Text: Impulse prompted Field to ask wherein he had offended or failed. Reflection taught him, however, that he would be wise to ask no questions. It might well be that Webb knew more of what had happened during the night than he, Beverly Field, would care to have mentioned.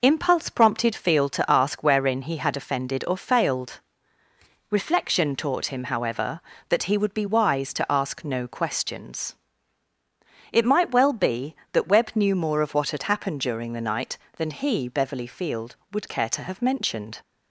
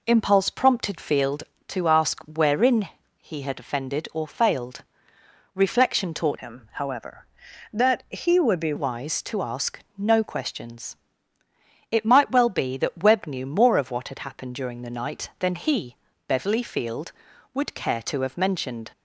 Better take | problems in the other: first | pauses between "wherein" and "he"; slight; at 2.8 s; 0.32 s long // changes voice from "him" to "be"; from 6.3 to 8.7 s; 2.4 s long // pauses between "ask" and "no"; slight; at 9.8 s; 0.16 s long

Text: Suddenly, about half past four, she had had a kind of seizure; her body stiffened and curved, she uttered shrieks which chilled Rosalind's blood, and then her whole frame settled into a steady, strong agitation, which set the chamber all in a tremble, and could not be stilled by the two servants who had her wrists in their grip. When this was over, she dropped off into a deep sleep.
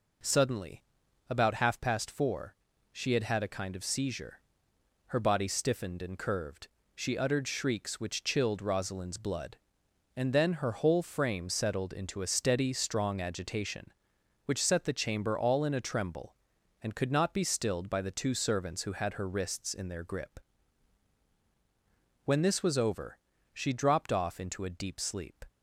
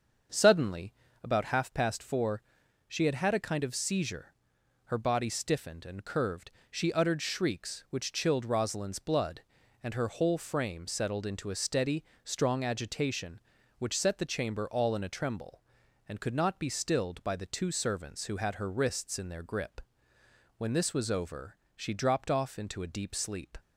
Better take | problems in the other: first | starts louder than the rest; until 1.6 s; 7 dB // skips "then"; at 9.9 s

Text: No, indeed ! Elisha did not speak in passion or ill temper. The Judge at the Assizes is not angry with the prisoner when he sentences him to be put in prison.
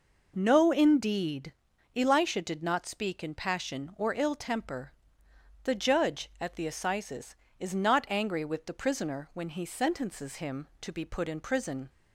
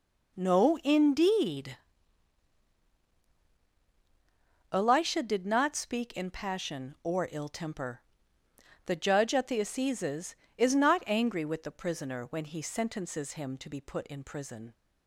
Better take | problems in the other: neither | none

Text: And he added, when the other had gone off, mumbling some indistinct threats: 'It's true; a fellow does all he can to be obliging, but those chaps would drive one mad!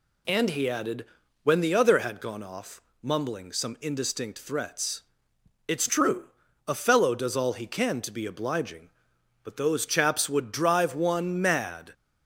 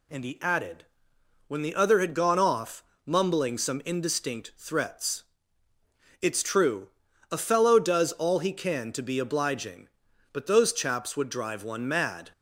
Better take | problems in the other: neither | none

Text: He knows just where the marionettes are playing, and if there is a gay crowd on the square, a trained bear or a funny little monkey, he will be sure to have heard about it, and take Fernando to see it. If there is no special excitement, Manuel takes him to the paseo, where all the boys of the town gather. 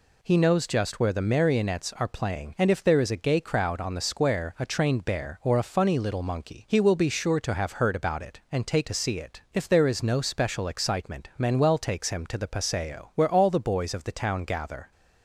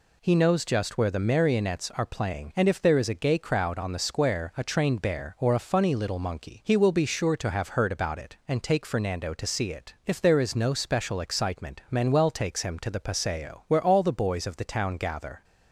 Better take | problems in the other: second | skips "Fernando"; at 8.8 s

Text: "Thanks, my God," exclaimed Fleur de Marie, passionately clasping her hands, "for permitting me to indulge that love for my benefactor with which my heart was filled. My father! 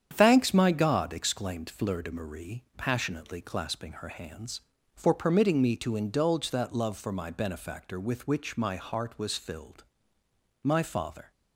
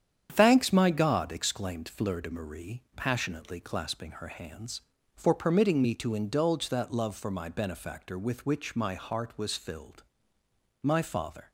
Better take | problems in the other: neither | starts louder than the rest; strong; the same in both

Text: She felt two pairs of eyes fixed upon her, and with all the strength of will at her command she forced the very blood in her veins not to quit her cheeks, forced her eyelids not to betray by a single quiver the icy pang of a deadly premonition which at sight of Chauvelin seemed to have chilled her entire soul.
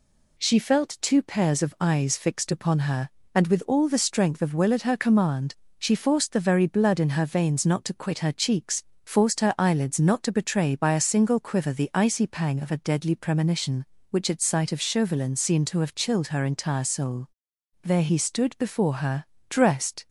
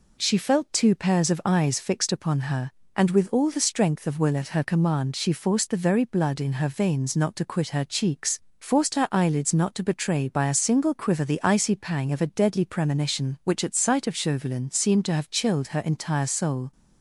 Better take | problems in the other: second | pauses between "command" and "she"; slight; at 5.5 s; 0.24 s long // goes on to say "There he stood before her dressed"; strong; from 17.8 s on; 2.2 s long

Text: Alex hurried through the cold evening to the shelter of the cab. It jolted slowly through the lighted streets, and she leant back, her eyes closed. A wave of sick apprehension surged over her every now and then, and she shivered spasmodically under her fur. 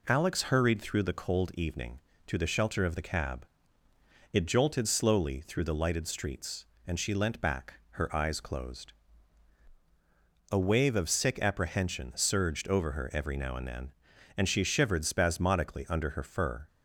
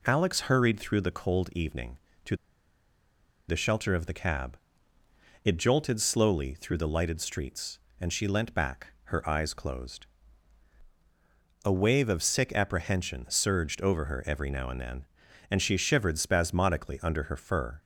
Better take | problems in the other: first | pauses between "to" and "the"; at 2.3 s; 1.1 s long

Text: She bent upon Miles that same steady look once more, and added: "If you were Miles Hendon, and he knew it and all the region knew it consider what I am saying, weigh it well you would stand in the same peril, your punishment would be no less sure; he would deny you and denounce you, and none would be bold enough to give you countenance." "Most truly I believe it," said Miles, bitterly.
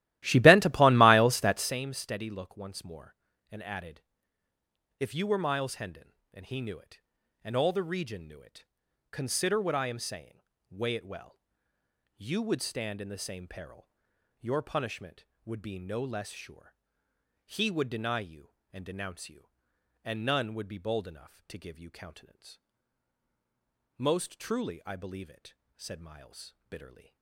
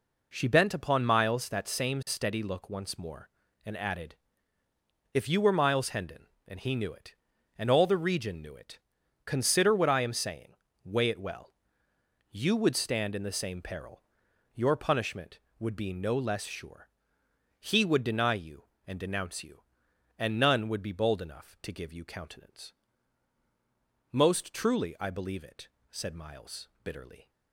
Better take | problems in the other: second | starts louder than the rest; strong; until 1.8 s; 15.5 dB // pauses between "it" and "consider"; noticeable; at 8.6 s; 0.46 s long; noticeable in the second // pauses between "well" and "you"; noticeable; at 11.3 s; 0.74 s long; noticeable in the second

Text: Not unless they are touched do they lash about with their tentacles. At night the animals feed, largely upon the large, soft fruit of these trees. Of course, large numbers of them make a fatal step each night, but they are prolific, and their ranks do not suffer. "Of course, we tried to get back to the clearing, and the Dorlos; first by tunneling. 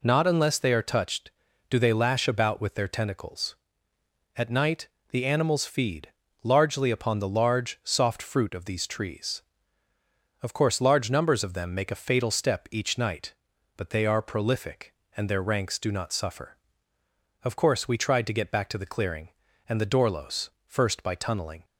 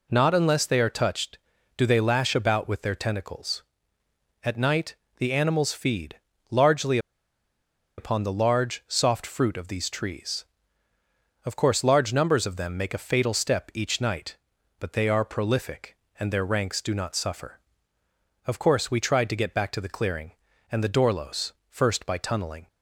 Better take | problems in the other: first | pauses between "night" and "the"; slight; at 4.9 s; 0.24 s long; slight in the first // pauses between "largely" and "upon"; at 6.9 s; 0.99 s long

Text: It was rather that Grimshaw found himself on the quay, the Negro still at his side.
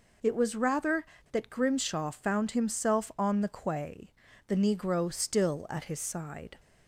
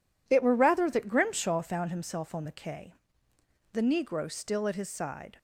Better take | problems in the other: first | says "were" for "was"; at 0.4 s

